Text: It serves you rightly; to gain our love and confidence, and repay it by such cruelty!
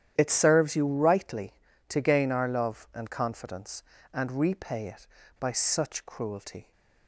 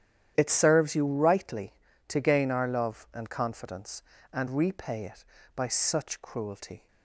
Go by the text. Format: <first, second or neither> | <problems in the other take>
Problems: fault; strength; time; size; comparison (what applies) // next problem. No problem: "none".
neither | starts louder than the rest; strong; the same in both